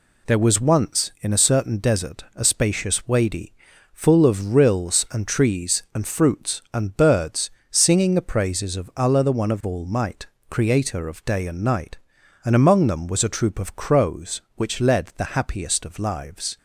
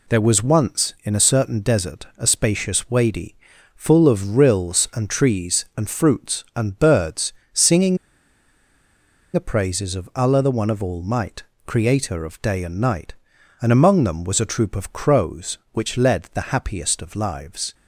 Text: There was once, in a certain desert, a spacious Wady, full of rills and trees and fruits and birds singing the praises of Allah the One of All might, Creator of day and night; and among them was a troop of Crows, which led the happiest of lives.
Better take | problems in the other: first | pauses between "birds" and "singing"; slight; at 7.3 s; 0.18 s long; slight in the first // pauses between "singing" and "the"; strong; at 7.9 s; 1.3 s long

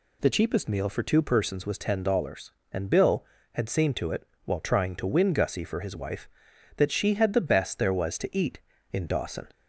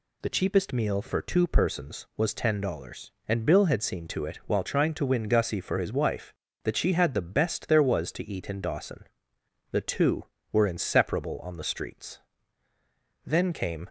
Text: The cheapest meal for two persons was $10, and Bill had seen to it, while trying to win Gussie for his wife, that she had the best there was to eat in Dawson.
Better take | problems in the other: first | goes on to say "The two were inseparable on the streets Then came"; strong; from 9.7 s on; 4.1 s long

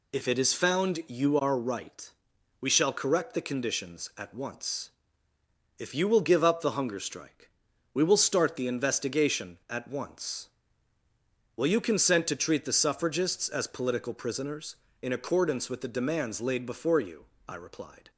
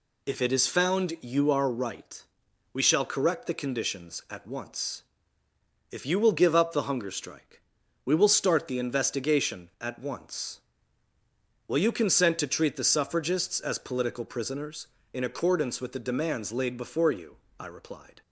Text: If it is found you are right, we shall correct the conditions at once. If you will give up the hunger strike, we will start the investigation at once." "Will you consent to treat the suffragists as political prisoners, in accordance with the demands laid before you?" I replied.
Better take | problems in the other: neither | none

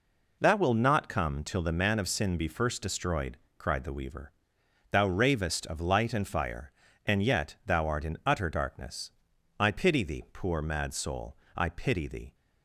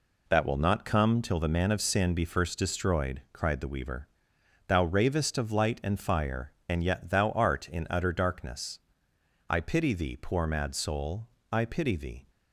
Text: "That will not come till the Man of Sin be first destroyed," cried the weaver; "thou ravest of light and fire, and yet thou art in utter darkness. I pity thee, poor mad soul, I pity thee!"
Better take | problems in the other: neither | none

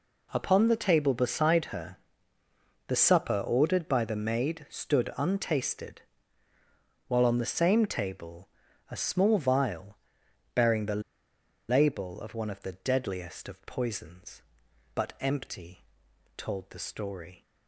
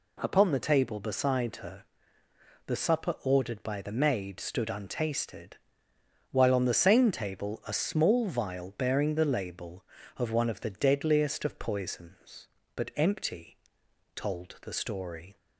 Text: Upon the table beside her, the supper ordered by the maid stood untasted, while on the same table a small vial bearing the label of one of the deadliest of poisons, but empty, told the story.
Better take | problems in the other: second | pauses between "table" and "a"; at 8.4 s; 0.44 s long // pauses between "vial" and "bearing"; noticeable; at 9.9 s; 0.56 s long // pauses between "the" and "label"; noticeable; at 11.0 s; 0.67 s long

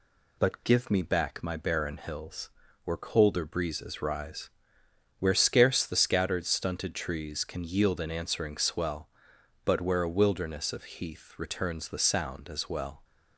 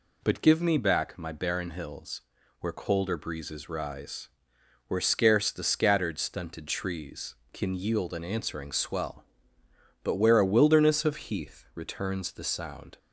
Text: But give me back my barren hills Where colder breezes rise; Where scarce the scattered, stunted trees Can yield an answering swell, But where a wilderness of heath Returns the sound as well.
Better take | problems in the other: first | pauses between "hills" and "Where"; at 2.2 s; 0.38 s long; slight in the first // stops before "as well"; at 12.9 s

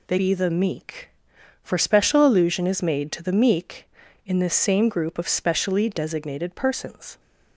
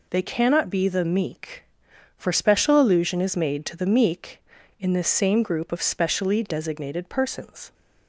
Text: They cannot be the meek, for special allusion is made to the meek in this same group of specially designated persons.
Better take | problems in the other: second | skips "cannot"; at 0.1 s

